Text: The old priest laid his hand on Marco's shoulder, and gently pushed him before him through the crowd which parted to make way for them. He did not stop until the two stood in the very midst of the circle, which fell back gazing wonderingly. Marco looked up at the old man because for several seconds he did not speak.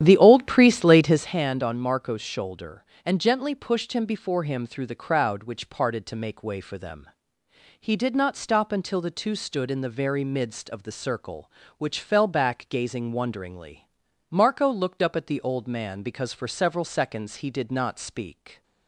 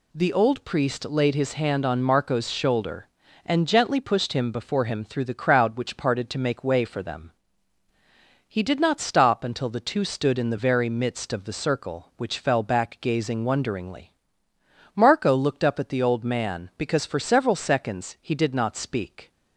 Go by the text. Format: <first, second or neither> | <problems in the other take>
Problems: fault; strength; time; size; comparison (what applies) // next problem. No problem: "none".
second | starts louder than the rest; strong; until 1.3 s; 10.5 dB